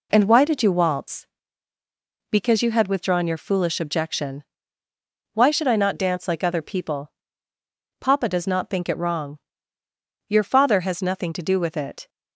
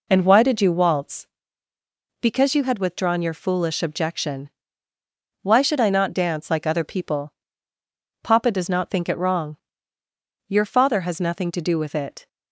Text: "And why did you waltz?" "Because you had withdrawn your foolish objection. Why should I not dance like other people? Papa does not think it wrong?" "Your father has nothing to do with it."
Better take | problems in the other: neither | none

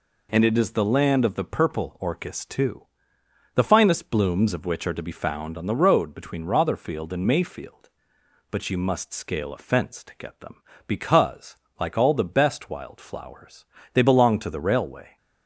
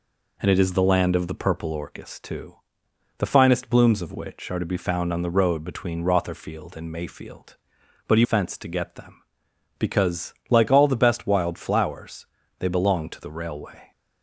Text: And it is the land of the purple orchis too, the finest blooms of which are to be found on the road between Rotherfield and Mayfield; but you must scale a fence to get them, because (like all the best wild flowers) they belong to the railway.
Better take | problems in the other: first | skips "must scale a"; at 8.2 s

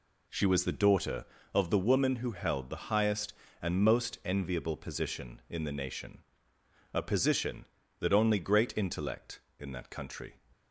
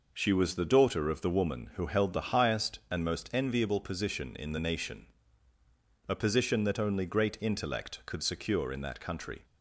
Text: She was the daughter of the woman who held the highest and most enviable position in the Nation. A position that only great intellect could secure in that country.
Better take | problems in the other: second | skips "could secure"; at 9.5 s

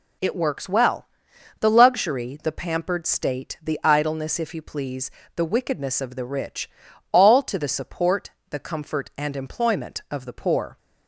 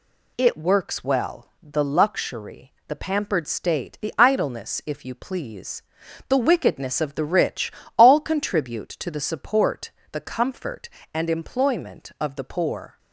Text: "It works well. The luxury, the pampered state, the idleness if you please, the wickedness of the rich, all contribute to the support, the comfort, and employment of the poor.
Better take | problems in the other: second | skips "contribute"; at 7.4 s

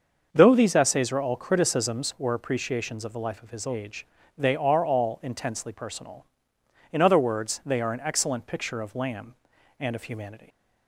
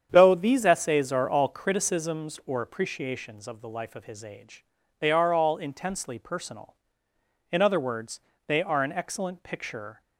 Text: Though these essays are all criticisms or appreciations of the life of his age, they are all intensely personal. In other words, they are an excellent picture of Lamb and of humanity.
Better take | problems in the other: first | starts louder than the rest; strong; until 1.1 s; 8 dB; also in the first // stops before "of Lamb and of humanity"; at 10.0 s

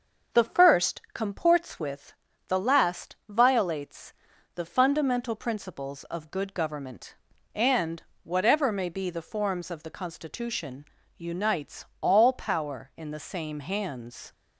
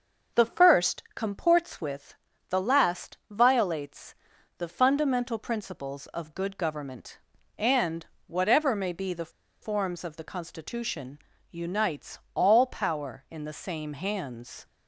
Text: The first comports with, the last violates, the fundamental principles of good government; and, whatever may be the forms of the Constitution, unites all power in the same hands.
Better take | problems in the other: first | starts louder than the rest; noticeable; until 1.4 s; 6 dB; noticeable in the first // pauses between "the" and "forms"; slight; at 9.2 s; 0.32 s long

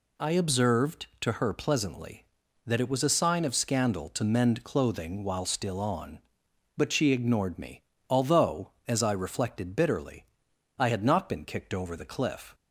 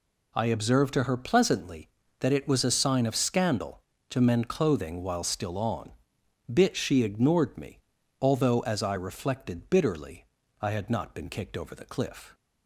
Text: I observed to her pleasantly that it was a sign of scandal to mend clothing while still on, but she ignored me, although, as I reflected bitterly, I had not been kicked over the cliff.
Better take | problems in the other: first | says "bit" for "but"; at 6.5 s

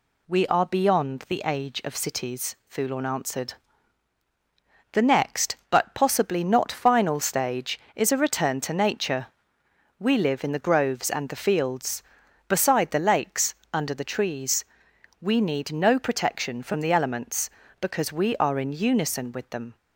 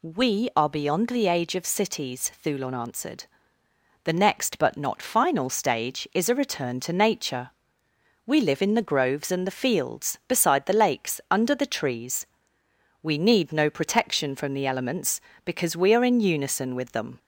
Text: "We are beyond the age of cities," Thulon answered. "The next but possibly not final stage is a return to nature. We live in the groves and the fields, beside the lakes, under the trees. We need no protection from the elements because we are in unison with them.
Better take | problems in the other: first | skips "possibly"; at 4.7 s

